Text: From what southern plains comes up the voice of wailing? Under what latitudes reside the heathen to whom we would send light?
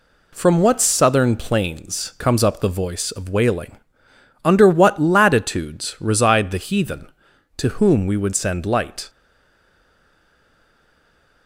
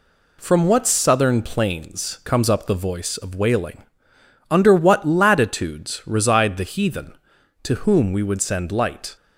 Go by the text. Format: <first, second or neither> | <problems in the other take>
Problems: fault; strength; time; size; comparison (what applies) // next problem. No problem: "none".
second | stays silent after the last word; from 9.0 s on; 2.4 s long